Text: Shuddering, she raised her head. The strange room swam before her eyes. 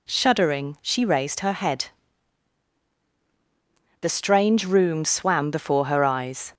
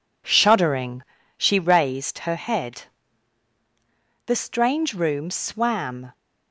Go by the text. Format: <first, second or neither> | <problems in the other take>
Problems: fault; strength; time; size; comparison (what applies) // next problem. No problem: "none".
first | stops before "before her eyes"; at 6.1 s